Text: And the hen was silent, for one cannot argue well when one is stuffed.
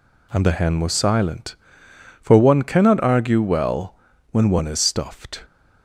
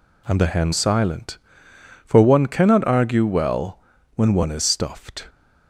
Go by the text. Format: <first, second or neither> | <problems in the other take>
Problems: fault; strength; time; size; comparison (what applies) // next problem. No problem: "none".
first | skips "was"; at 0.7 s // pauses between "well" and "when"; slight; at 3.7 s; 0.36 s long; slight in the first